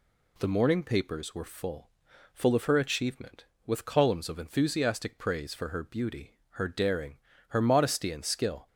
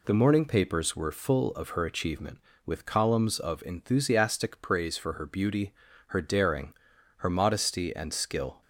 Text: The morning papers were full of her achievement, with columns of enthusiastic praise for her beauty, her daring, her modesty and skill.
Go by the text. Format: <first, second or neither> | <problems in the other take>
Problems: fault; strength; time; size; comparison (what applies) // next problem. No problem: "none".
second | says "full" twice; at 2.3 s